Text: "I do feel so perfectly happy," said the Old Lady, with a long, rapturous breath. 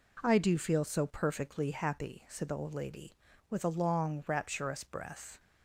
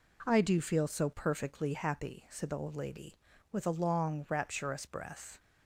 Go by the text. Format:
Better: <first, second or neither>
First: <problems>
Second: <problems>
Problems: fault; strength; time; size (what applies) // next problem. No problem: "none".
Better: neither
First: none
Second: none